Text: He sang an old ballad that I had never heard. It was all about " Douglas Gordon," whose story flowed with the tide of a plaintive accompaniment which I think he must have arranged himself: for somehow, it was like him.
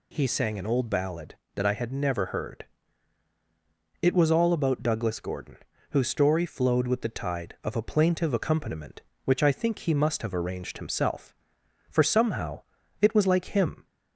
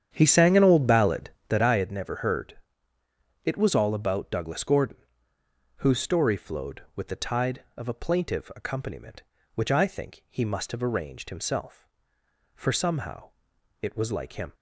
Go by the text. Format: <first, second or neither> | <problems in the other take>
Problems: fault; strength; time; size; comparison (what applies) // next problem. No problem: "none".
first | starts louder than the rest; strong; until 1.7 s; 9 dB